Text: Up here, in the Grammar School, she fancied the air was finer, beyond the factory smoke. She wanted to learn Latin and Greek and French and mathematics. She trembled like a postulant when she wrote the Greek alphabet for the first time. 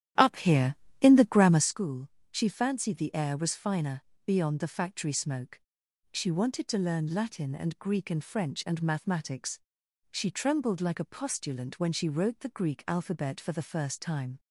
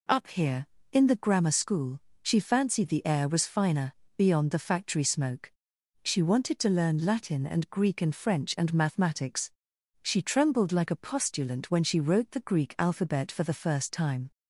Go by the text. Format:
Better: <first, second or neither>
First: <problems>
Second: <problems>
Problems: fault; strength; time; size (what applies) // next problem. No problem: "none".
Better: second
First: starts louder than the rest; strong; until 1.7 s; 11.5 dB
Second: none